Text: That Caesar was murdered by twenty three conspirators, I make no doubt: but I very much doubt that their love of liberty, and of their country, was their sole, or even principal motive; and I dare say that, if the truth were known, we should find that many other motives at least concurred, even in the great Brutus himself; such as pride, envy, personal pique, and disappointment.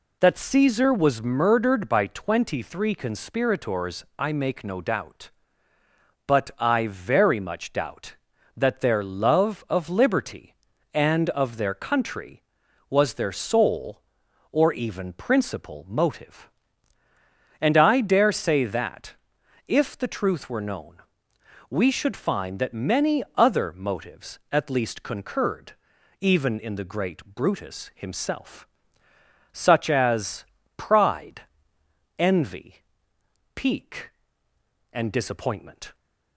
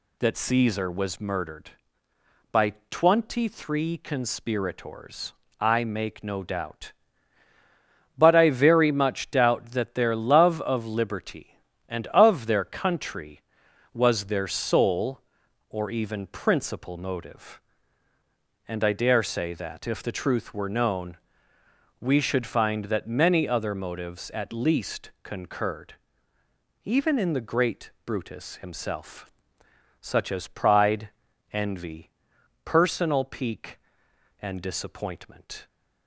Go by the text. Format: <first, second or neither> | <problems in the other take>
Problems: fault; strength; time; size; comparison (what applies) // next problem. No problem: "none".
second | pauses between "as" and "pride"; slight; at 30.4 s; 0.32 s long // skips "personal"; at 33.1 s